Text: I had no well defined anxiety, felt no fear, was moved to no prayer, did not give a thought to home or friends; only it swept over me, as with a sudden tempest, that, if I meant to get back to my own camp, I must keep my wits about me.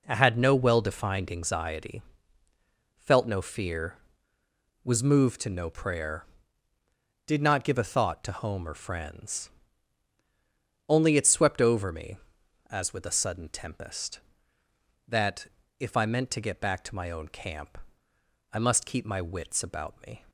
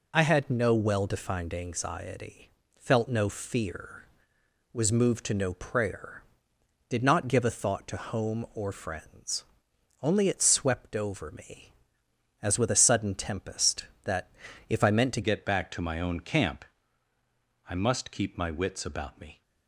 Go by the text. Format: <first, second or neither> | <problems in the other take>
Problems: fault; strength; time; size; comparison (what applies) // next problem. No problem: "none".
first | changes voice at "get"; from 15.2 s on; 4.2 s long